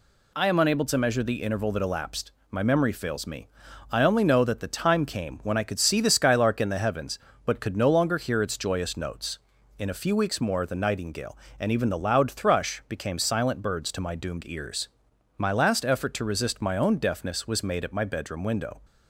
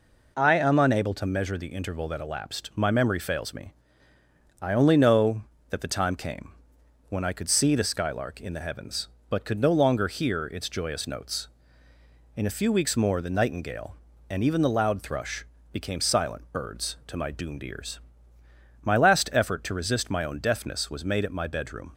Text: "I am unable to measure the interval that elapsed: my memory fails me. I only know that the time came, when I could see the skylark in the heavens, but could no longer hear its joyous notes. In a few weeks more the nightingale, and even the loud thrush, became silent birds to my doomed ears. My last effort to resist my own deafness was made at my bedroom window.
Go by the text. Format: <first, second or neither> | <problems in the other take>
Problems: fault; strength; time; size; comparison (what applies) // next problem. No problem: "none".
first | stops before "window"; at 21.9 s